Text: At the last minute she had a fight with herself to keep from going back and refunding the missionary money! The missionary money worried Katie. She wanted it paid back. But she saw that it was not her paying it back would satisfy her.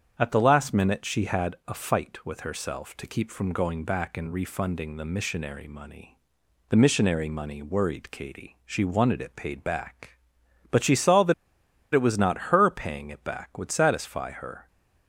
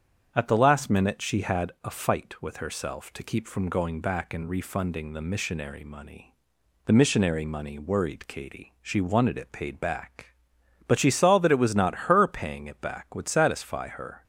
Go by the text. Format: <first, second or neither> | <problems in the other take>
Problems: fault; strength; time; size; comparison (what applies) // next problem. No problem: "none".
second | starts louder than the rest; strong; until 1.1 s; 8 dB; strong in the second // pauses between "that" and "it"; noticeable; at 11.3 s; 0.60 s long